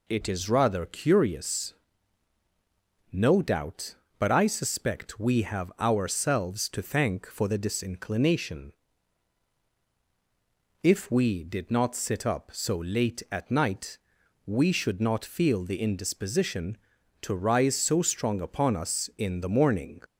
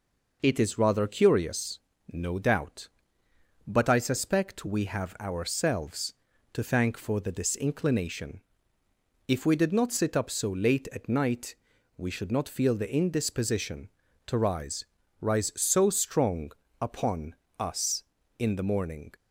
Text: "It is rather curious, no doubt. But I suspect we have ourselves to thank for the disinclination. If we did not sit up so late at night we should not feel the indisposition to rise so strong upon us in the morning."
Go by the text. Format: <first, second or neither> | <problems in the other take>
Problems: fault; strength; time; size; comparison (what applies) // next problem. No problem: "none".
first | pauses between "night" and "we"; at 11.5 s; 0.42 s long; noticeable in the first // says "rise" twice; at 15.1 s // pauses between "strong" and "upon"; slight; at 16.5 s; 0.28 s long // pauses between "upon" and "us"; slight; at 17.3 s; 0.24 s long